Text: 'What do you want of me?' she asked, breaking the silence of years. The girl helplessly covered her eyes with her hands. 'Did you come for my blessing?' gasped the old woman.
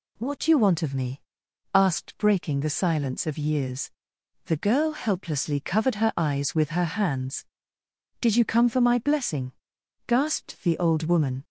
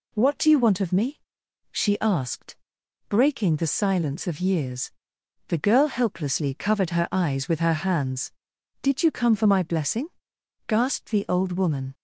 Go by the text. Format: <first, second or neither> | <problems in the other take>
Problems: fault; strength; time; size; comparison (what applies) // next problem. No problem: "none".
second | skips "she"; at 1.4 s